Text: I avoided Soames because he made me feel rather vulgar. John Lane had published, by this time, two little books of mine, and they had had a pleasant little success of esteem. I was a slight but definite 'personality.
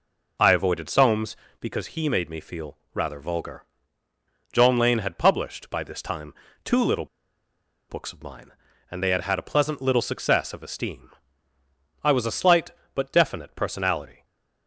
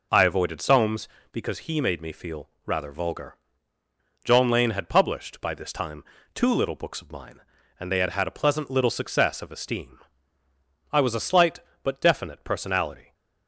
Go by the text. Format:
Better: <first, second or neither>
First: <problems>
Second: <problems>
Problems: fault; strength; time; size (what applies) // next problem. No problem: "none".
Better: second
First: pauses between "feel" and "rather"; slight; at 2.7 s; 0.16 s long // pauses between "little" and "books"; noticeable; at 7.0 s; 0.83 s long // stays silent after the last word; slight; from 14.1 s on; 0.5 s long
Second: pauses between "feel" and "rather"; slight; at 2.4 s; 0.16 s long